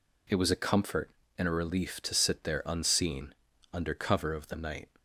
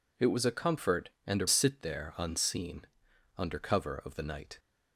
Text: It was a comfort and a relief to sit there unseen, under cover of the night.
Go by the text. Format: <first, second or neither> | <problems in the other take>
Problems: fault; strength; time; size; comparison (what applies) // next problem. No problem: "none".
first | skips "relief to"; at 1.4 s